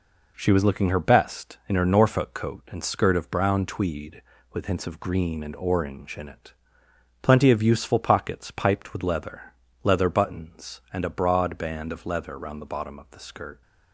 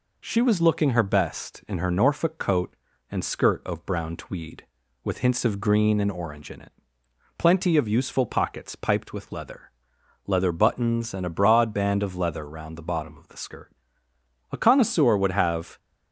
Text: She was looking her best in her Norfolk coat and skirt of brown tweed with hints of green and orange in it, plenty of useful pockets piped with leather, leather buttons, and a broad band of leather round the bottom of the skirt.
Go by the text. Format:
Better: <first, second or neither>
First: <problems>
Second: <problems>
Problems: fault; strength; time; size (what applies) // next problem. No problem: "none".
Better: first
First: none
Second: goes on to say "A connoisseur would have"; noticeable; from 14.4 s on; 1.2 s long